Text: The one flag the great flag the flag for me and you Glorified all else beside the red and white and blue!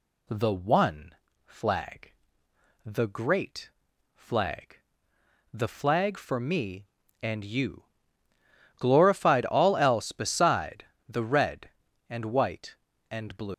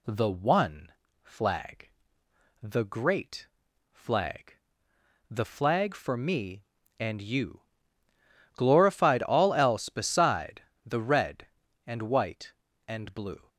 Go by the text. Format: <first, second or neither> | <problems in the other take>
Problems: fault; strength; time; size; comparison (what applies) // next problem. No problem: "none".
second | pauses between "one" and "flag"; slight; at 1.1 s; 0.30 s long; slight in the second // pauses between "flag" and "the"; noticeable; at 2.1 s; 0.74 s long; noticeable in the second // pauses between "great" and "flag"; at 3.6 s; 0.44 s long; also in the second // pauses between "flag" and "the"; noticeable; at 4.7 s; 0.76 s long; noticeable in the second // pauses between "you" and "Glorified"; noticeable; at 7.8 s; 0.94 s long; noticeable in the second // pauses between "beside" and "the"; slight; at 10.8 s; 0.24 s long; slight in the second // leaves "blue" unfinished; at 13.5 s; 170 ms